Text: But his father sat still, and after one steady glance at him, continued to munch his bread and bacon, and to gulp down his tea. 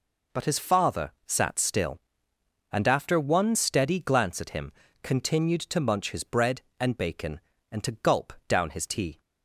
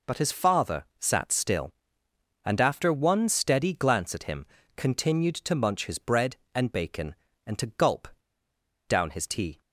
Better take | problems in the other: first | pauses between "gulp" and "down"; noticeable; at 8.0 s; 0.80 s long

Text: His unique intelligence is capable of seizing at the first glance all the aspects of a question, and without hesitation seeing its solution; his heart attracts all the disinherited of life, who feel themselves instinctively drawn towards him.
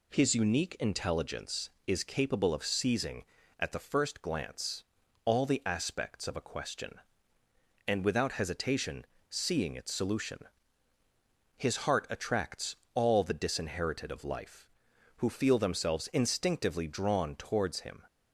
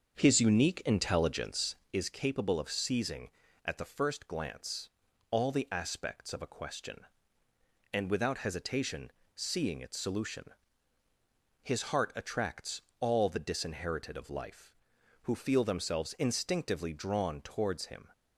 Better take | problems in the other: first | starts louder than the rest; until 1.9 s; 7 dB // pauses between "glance" and "all"; at 4.8 s; 0.40 s long; also in the first // pauses between "hesitation" and "seeing"; slight; at 9.1 s; 0.24 s long; slight in the first // pauses between "attracts" and "all"; slight; at 12.8 s; 0.20 s long; slight in the first

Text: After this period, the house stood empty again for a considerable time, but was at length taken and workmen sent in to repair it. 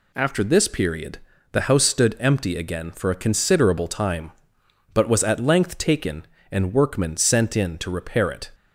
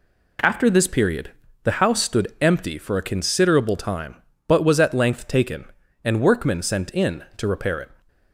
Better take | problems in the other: first | skips "again"; at 2.7 s

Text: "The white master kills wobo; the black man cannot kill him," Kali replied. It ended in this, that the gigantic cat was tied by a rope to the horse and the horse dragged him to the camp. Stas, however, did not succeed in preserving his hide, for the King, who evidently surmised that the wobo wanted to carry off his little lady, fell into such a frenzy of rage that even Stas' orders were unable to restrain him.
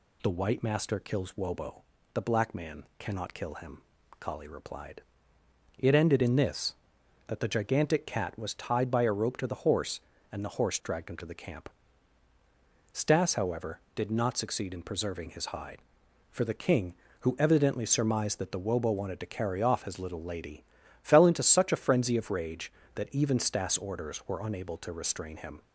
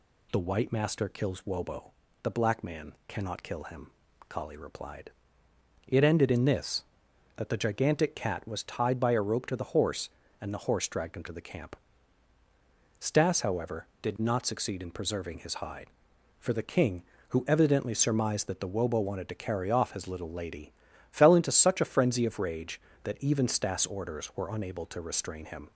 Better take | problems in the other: neither | none

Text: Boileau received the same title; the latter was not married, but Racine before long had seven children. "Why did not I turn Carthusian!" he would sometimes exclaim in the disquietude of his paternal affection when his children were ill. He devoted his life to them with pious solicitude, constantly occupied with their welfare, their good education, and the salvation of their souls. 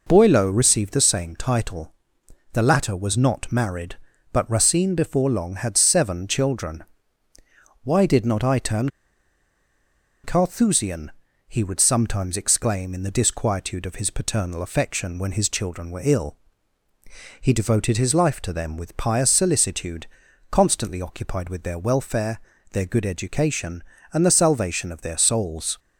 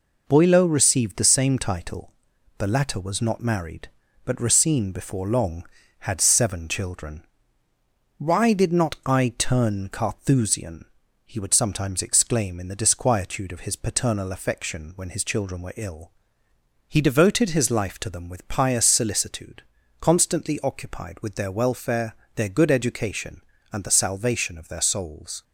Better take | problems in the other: second | pauses between "turn" and "Carthusian"; strong; at 8.8 s; 1.3 s long

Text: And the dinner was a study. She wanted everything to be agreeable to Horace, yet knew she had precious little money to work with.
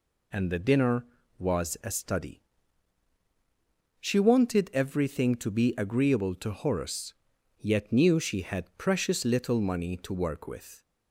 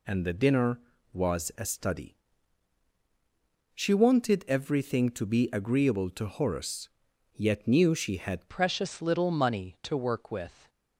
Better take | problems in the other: first | changes voice at "precious"; from 8.4 s on; 2.2 s long

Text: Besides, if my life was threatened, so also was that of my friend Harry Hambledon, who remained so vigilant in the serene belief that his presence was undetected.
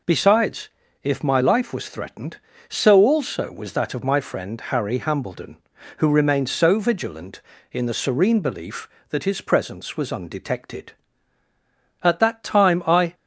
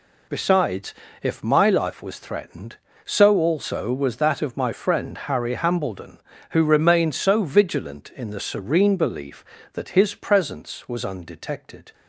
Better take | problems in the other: second | goes on to say "At that time I"; noticeable; from 12.0 s on; 1.1 s long

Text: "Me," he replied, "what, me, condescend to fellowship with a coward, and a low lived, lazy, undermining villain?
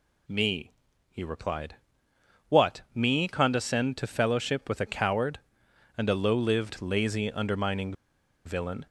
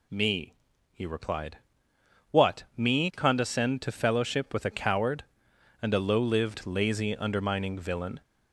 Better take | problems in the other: second | pauses between "undermining" and "villain"; noticeable; at 7.9 s; 0.53 s long

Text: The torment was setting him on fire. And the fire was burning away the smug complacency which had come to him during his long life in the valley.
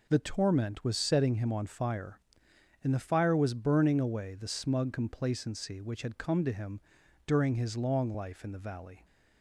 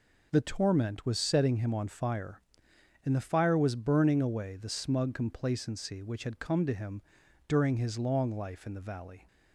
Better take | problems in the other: neither | pauses between "him" and "during"; the same in both

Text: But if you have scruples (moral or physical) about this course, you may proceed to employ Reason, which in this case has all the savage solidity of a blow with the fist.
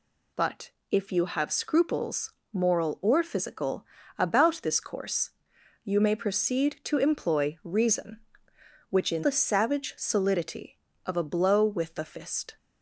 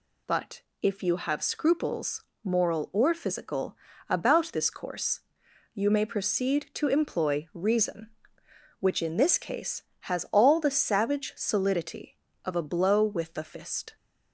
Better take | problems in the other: second | pauses between "But" and "if"; slight; at 0.7 s; 0.20 s long; slight in the second // skips "this case has all"; at 9.2 s

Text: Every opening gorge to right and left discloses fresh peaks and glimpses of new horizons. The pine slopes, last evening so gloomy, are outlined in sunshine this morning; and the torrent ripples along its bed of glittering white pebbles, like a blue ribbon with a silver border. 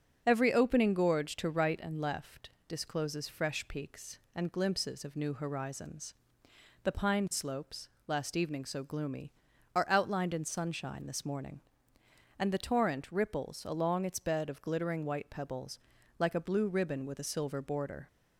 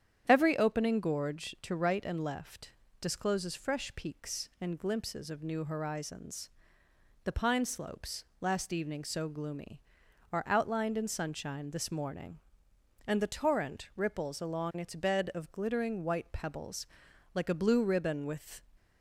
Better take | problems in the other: first | starts louder than the rest; strong; until 1.2 s; 9 dB; also in the first // pauses between "left" and "discloses"; slight; at 2.7 s; 0.28 s long; slight in the first // stops before "a silver border"; at 18.7 s

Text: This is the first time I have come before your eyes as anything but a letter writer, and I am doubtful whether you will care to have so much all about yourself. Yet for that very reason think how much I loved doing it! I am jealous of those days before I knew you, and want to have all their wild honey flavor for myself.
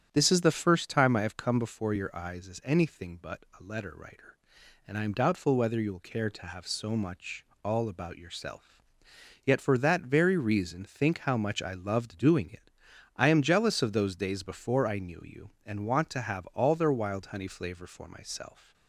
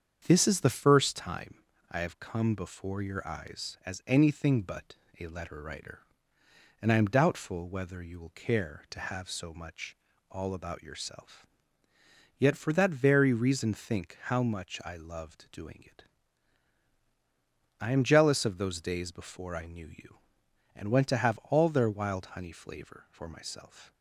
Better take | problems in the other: first | starts louder than the rest; strong; until 1.2 s; 7.5 dB; strong in the first // pauses between "time" and "I"; slight; at 1.5 s; 0.36 s long // pauses between "but" and "a"; slight; at 4.9 s; 0.22 s long; slight in the first // pauses between "much" and "all"; slight; at 9.9 s; 0.34 s long; slight in the first // says "went" for "want"; at 20.9 s

